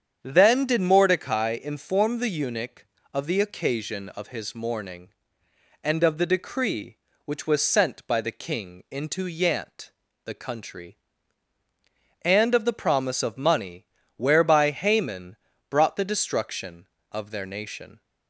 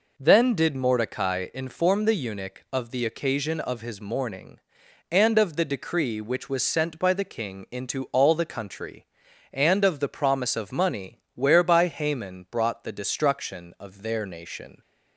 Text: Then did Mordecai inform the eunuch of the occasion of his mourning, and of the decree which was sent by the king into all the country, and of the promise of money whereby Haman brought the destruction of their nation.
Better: second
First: starts louder than the rest; strong; until 1.2 s; 8 dB // says "yant" for "all"; at 9.2 s // pauses between "money" and "whereby"; slight; at 13.8 s; 0.32 s long // pauses between "Haman" and "brought"; slight; at 15.3 s; 0.32 s long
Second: none

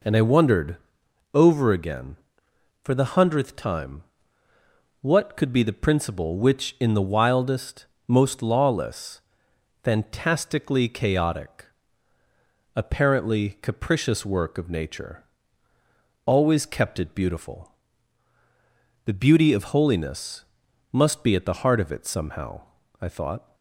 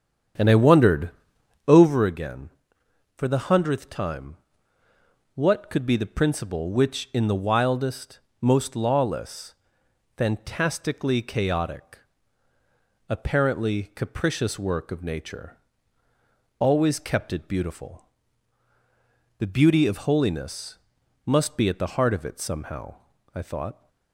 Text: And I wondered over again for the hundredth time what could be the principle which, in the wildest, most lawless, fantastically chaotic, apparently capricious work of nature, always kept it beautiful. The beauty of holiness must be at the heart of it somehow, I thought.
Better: first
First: pauses between "wondered" and "over"; noticeable; at 0.7 s; 0.56 s long // pauses between "time" and "what"; noticeable; at 4.0 s; 0.98 s long // pauses between "holiness" and "must"; noticeable; at 20.4 s; 0.48 s long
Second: starts louder than the rest; strong; until 2.0 s; 8.5 dB // pauses between "wondered" and "over"; noticeable; at 1.1 s; 0.56 s long // pauses between "time" and "what"; noticeable; at 4.3 s; 0.98 s long // pauses between "holiness" and "must"; noticeable; at 20.7 s; 0.48 s long

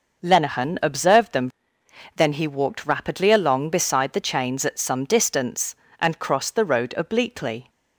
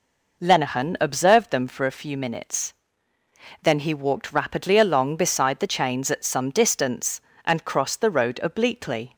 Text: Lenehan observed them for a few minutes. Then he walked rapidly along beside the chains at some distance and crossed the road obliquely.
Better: second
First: skips "for a few minutes"; at 1.8 s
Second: none

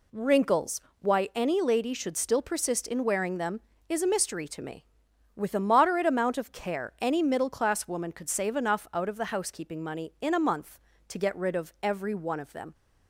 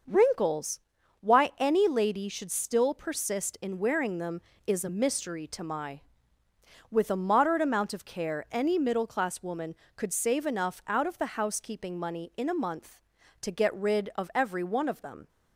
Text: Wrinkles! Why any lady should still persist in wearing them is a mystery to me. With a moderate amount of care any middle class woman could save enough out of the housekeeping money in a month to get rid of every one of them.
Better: first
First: none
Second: starts louder than the rest; noticeable; until 1.4 s; 6 dB // says "my" for "me"; at 5.6 s

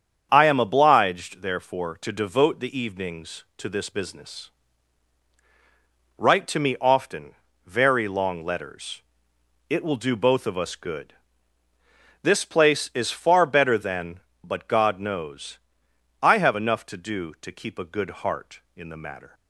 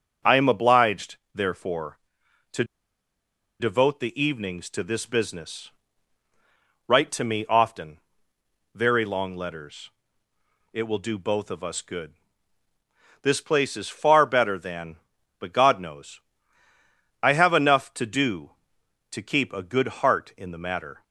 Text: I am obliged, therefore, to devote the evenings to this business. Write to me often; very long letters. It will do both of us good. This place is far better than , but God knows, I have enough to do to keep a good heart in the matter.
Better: first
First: starts louder than the rest; strong; until 1.3 s; 7.5 dB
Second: starts louder than the rest; until 1.4 s; 6.5 dB // pauses between "to" and "devote"; noticeable; at 2.6 s; 0.96 s long

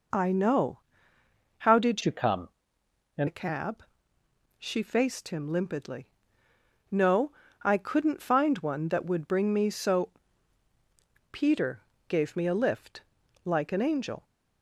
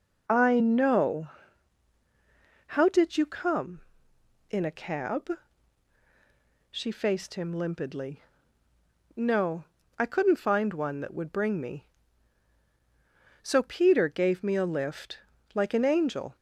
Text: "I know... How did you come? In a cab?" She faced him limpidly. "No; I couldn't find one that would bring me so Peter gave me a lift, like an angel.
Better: second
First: changes voice from "you" to "In"; from 2.0 to 3.2 s; 1.2 s long // pauses between "so" and "Peter"; at 10.0 s; 1.2 s long // pauses between "Peter" and "gave"; slight; at 11.8 s; 0.26 s long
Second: none

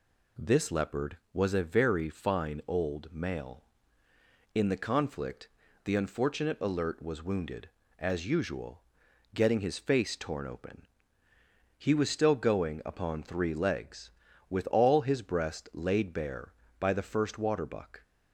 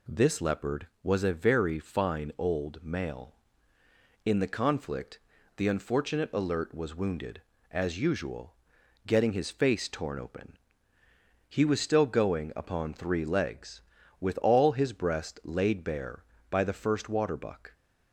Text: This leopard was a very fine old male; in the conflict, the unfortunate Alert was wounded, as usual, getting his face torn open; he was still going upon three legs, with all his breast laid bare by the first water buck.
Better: neither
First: none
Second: none

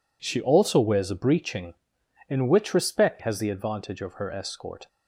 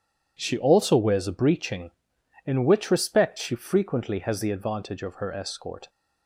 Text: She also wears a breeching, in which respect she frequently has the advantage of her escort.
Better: second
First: skips "she frequently"; at 3.1 s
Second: none

